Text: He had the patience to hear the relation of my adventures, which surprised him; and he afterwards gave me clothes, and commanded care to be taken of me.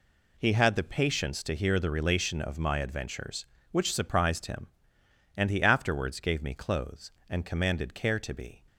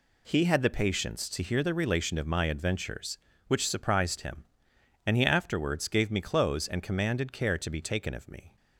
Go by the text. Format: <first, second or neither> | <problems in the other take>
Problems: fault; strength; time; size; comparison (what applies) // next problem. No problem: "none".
second | stops before "taken of me"; at 8.6 s